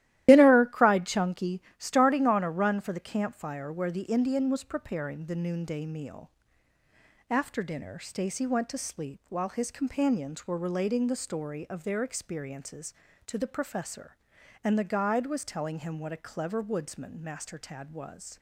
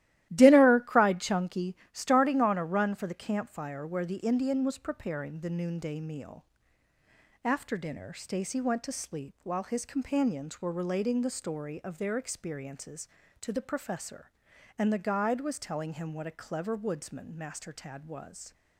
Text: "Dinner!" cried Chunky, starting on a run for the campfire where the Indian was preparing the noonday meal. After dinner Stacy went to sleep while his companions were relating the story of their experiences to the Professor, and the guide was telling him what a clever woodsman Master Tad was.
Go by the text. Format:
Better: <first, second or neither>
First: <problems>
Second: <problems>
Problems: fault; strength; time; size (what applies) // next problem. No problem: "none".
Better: second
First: loses the start of "Dinner"; at 0.2 s; 125 ms // starts louder than the rest; strong; until 1.2 s; 14 dB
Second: starts louder than the rest; strong; until 1.3 s; 14.5 dB